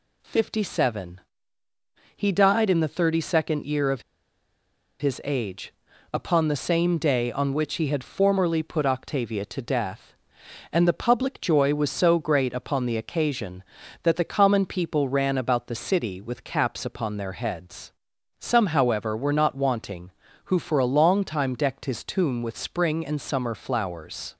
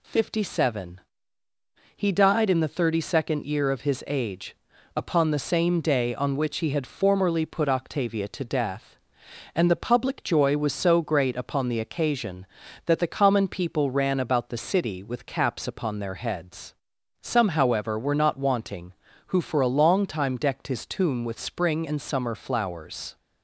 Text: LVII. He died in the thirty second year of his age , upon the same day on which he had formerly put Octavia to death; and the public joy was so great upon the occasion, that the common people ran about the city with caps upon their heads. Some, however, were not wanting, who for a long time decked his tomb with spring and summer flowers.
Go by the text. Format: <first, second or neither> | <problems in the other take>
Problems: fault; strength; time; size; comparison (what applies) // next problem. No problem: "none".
second | pauses between "of" and "his"; noticeable; at 4.0 s; 0.97 s long